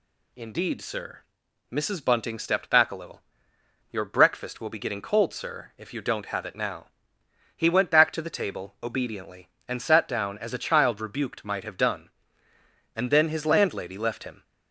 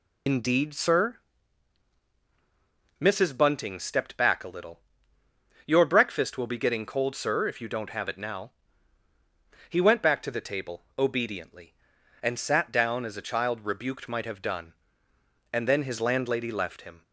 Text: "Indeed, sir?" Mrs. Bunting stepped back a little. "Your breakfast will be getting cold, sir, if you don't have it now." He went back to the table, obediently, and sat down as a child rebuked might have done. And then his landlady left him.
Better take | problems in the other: first | loses the start of "Indeed"; at 0.2 s; 80 ms

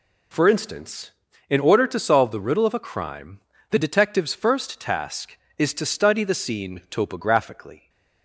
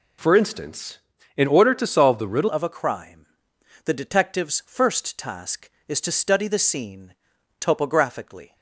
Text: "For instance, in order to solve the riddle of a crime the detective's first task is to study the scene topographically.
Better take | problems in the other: first | changes voice at "of"; from 2.4 s on; 6.1 s long // pauses between "crime" and "the"; noticeable; at 3.2 s; 0.58 s long; slight in the first // pauses between "scene" and "topographically"; noticeable; at 7.1 s; 0.46 s long

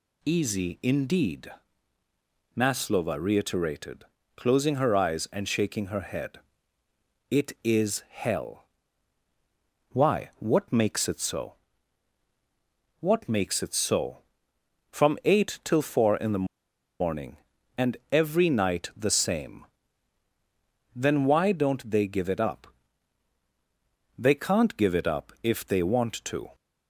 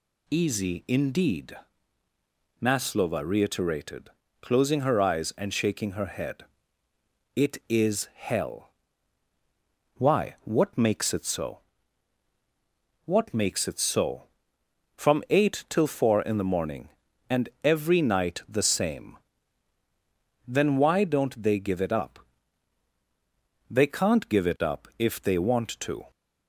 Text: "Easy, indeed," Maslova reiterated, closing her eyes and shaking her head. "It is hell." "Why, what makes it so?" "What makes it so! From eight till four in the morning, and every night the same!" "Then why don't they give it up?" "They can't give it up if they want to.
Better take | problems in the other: second | pauses between "the" and "morning"; noticeable; at 16.4 s; 0.54 s long

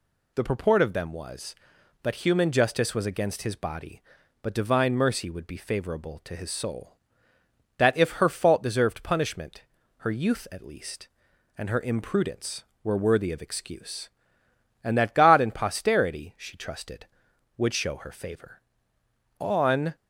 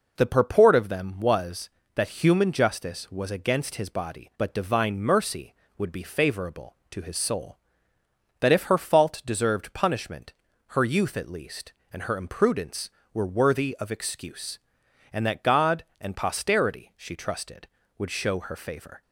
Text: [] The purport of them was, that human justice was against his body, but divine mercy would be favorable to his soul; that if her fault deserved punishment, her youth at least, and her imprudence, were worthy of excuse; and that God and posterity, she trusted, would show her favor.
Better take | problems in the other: second | goes on to say "On"; from 19.3 s on; 0.58 s long

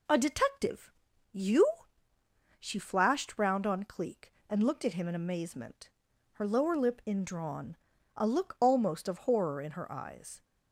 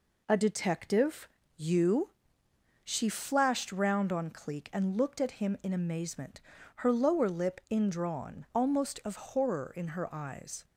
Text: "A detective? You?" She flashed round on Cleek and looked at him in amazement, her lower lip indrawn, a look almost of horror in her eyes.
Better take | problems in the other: first | skips "a look"; at 8.5 s

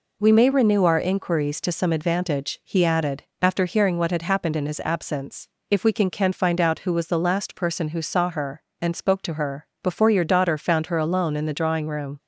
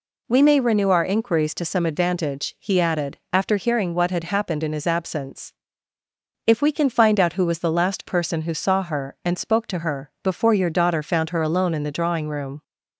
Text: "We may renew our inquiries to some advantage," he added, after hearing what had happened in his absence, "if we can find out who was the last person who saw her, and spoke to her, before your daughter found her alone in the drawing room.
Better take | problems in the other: second | says "can" twice; at 6.0 s

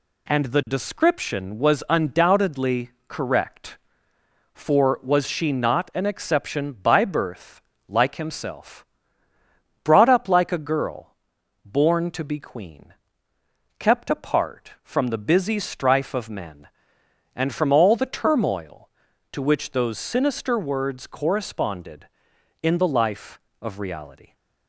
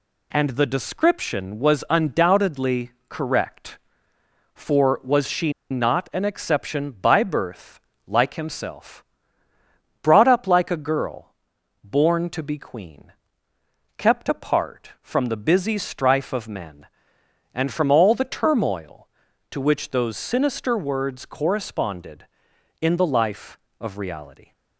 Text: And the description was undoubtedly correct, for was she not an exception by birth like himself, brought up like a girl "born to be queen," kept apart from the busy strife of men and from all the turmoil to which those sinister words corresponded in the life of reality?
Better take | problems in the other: first | pauses between "undoubtedly" and "correct"; slight; at 2.9 s; 0.18 s long; slight in the first // pauses between "she" and "not"; slight; at 5.5 s; 0.19 s long // pauses between "birth" and "like"; slight; at 7.7 s; 0.28 s long; slight in the first // pauses between "girl" and "born"; noticeable; at 11.3 s; 0.50 s long; noticeable in the first

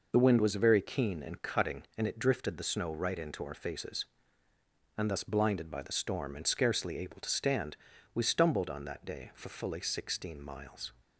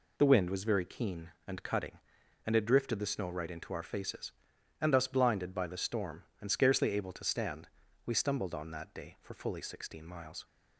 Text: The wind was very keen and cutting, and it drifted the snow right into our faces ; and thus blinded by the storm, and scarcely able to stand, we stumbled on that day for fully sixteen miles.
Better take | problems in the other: neither | none

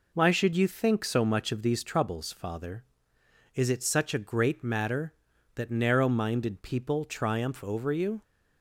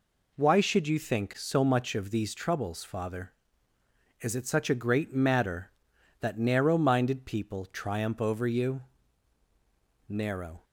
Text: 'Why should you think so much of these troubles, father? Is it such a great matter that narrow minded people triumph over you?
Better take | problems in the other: first | goes on to say "Narrow"; from 10.0 s on; 0.54 s long

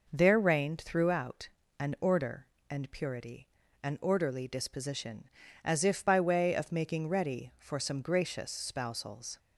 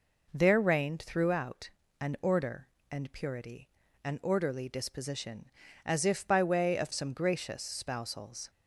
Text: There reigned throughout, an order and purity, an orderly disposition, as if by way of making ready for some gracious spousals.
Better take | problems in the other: first | skips "making ready for"; at 6.9 s

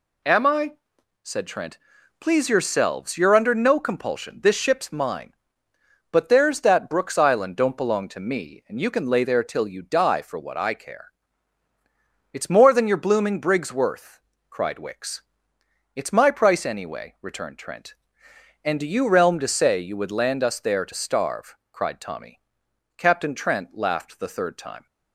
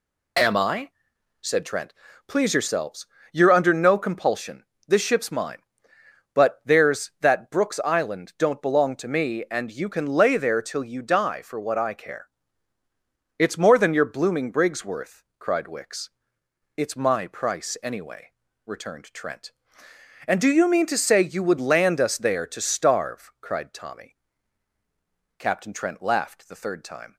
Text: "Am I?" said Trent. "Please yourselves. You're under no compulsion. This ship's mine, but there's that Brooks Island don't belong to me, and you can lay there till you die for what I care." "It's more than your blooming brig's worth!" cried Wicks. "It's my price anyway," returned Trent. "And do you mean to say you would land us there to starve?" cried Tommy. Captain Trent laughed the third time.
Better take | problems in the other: second | says "realm" for "mean"; at 19.0 s

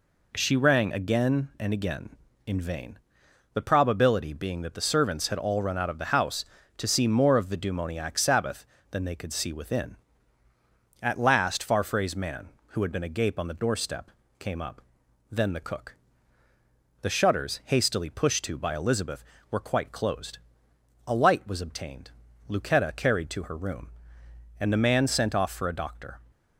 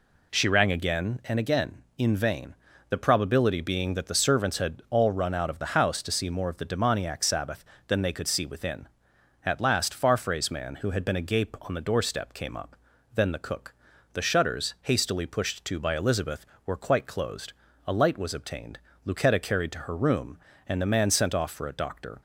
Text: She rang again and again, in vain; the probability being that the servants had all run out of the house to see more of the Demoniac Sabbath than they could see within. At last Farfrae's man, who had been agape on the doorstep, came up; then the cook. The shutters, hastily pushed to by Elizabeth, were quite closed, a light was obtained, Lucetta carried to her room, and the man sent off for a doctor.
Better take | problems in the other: neither | none

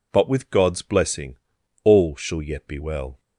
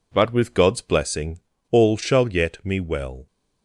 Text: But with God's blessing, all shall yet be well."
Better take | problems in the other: first | says "me" for "be"; at 2.6 s

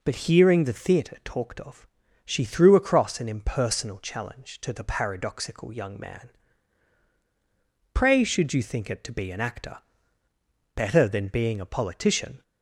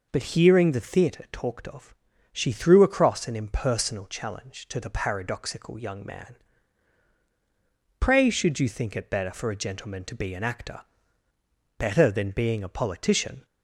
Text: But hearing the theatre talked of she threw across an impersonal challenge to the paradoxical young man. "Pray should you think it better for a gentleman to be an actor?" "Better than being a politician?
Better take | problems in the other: second | pauses between "of" and "she"; at 1.8 s; 0.38 s long; also in the second // skips "better for a gentleman"; at 9.0 s

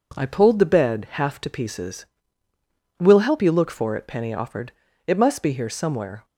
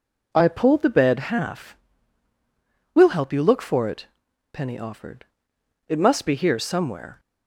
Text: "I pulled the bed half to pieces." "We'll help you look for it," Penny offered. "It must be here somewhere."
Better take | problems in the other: first | skips "to pieces"; at 2.3 s

